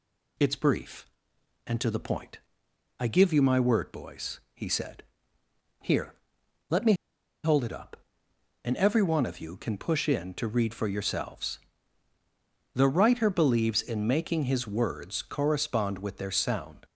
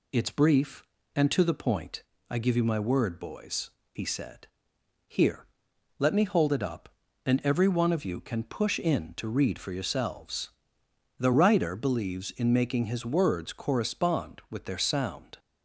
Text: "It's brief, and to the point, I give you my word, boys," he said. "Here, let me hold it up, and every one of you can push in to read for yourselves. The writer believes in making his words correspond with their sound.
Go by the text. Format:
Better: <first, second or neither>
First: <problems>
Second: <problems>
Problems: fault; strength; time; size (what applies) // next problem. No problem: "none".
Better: second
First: pauses between "me" and "hold"; noticeable; at 6.9 s; 0.50 s long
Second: none